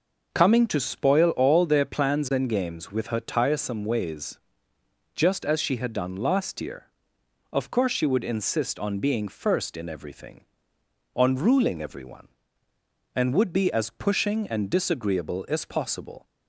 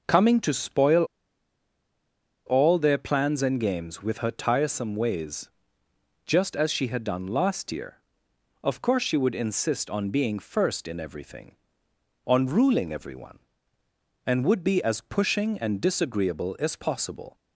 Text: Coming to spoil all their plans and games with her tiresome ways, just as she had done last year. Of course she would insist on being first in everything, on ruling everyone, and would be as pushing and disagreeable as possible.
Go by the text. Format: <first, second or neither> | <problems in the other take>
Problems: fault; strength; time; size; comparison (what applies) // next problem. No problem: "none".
first | pauses between "spoil" and "all"; strong; at 1.0 s; 1.4 s long